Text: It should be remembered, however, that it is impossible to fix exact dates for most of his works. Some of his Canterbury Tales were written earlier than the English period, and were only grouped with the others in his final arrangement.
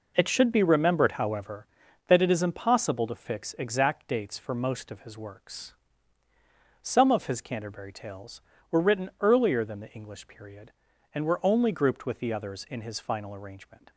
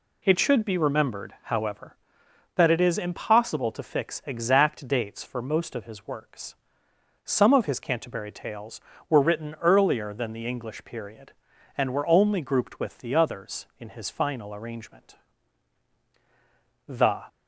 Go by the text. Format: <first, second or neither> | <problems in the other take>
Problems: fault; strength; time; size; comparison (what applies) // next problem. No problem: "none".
first | goes on to say "The"; slight; from 16.8 s on; 0.38 s long